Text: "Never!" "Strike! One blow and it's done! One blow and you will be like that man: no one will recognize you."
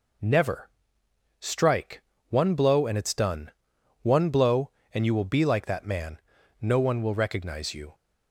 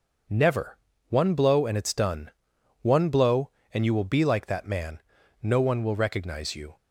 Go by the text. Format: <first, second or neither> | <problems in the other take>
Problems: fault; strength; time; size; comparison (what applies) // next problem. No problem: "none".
first | skips "Strike"; at 0.9 s